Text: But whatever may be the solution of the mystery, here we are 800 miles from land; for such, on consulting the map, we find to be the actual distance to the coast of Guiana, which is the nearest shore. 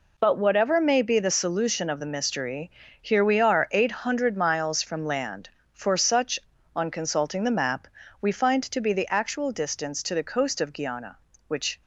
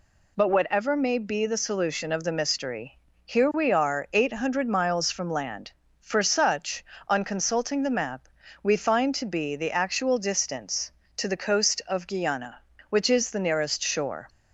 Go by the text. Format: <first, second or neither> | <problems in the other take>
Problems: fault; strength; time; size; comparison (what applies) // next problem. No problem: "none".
second | stops before "is the nearest shore"; at 11.8 s